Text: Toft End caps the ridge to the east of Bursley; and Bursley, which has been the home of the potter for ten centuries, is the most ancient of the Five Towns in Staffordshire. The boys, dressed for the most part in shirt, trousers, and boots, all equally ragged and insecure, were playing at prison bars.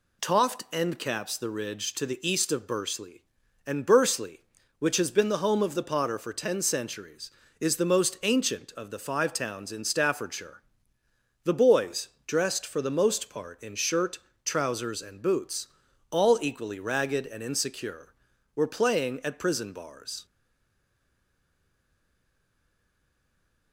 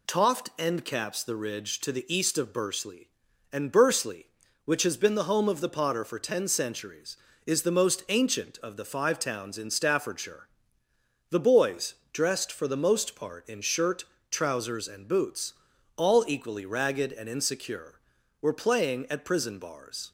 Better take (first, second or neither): second